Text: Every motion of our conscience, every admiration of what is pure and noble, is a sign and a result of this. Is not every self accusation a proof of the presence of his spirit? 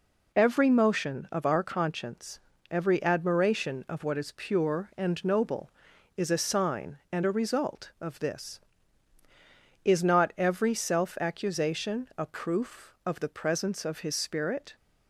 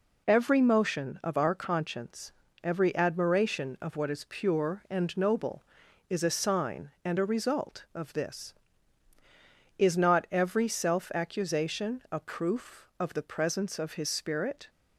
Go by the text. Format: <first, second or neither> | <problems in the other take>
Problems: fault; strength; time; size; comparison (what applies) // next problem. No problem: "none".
neither | none